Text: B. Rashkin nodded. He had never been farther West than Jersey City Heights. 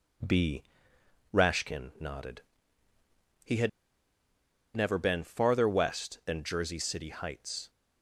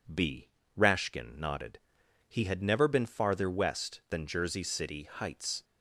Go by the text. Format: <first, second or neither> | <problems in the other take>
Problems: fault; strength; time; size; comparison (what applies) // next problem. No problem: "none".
second | pauses between "had" and "never"; at 3.6 s; 1.0 s long